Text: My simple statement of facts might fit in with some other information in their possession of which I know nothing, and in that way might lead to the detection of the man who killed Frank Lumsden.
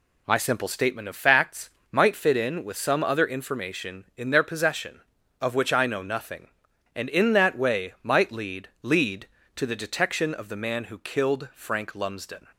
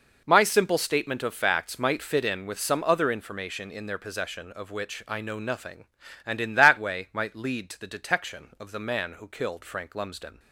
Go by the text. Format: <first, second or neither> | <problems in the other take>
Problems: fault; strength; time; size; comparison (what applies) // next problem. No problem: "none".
second | pauses between "facts" and "might"; slight; at 1.6 s; 0.20 s long // says "lead" twice; at 8.8 s